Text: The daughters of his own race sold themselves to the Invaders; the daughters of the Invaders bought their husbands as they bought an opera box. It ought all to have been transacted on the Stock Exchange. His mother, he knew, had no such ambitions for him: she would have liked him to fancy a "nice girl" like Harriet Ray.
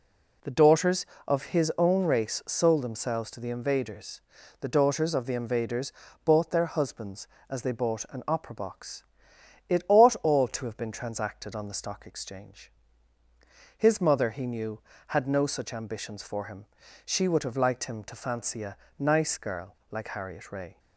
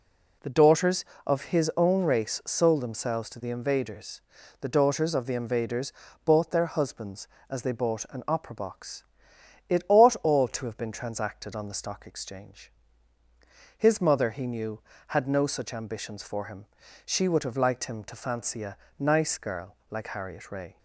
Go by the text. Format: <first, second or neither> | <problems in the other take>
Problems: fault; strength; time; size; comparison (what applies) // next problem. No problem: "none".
neither | pauses between "Invaders" and "bought"; slight; the same in both // pauses between "a" and "nice"; slight; the same in both